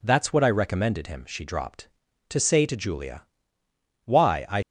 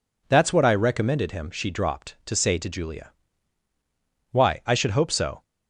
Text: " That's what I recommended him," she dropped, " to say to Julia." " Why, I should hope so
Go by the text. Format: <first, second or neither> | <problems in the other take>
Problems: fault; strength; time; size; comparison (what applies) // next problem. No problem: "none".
second | stops before "should hope so"; at 4.6 s